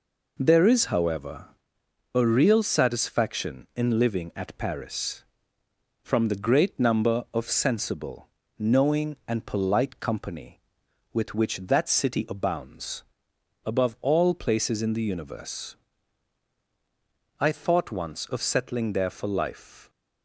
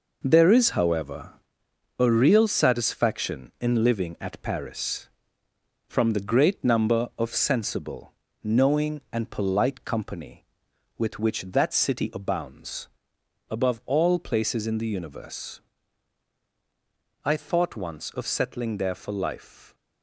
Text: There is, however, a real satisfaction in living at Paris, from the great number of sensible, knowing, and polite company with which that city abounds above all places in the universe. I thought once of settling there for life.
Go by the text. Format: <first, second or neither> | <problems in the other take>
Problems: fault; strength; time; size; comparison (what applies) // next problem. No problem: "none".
first | gets quieter; strong; throughout; 8.5 dB // pauses between "abounds" and "above"; noticeable; at 12.8 s; 0.64 s long; noticeable in the first